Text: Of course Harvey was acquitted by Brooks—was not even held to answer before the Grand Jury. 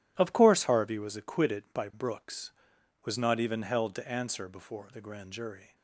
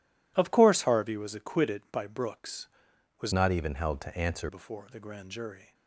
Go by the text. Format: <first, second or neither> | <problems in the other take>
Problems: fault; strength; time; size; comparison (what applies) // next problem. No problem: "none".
first | changes voice from "not" to "answer"; from 3.3 to 4.4 s; 1.1 s long